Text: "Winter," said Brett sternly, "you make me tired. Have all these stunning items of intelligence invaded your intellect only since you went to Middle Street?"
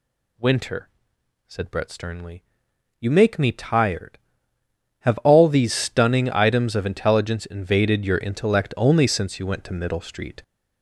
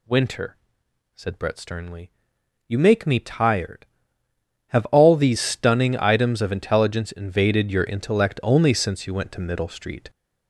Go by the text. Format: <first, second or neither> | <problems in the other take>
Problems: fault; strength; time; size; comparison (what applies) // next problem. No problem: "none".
neither | none